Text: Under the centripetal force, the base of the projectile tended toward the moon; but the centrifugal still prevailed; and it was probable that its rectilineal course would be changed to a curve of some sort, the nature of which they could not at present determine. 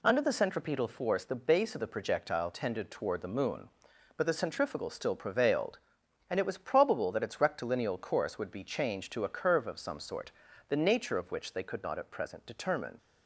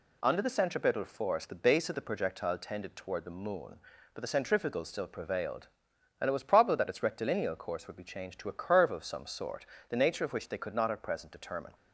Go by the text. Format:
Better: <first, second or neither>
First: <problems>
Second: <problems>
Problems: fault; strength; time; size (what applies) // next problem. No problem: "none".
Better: neither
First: none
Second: none